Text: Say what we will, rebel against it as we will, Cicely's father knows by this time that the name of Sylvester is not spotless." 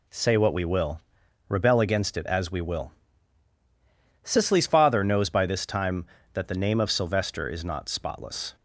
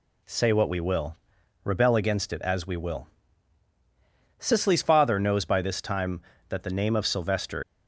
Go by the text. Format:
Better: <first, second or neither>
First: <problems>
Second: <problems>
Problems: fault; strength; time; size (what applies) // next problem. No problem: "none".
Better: first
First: none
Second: stops before "is not spotless"; at 7.6 s